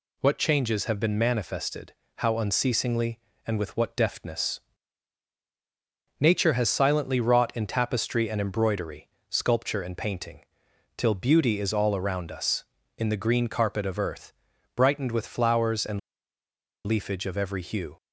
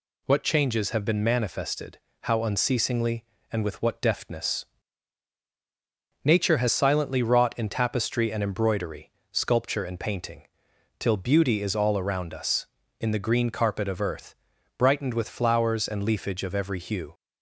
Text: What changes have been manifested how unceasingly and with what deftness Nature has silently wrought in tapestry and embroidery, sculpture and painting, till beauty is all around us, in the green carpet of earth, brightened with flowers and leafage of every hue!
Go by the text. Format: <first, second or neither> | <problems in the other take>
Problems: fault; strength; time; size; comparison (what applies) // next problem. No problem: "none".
second | pauses between "manifested" and "how"; slight; at 1.9 s; 0.22 s long; slight in the second // pauses between "deftness" and "Nature"; strong; at 4.5 s; 1.6 s long; strong in the second // pauses between "and" and "leafage"; noticeable; at 15.9 s; 0.86 s long